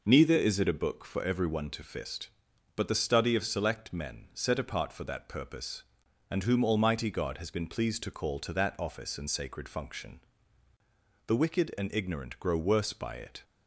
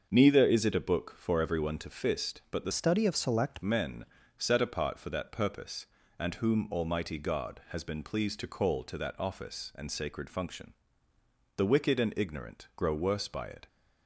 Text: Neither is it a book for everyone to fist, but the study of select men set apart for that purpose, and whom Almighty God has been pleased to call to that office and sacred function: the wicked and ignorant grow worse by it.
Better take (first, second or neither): first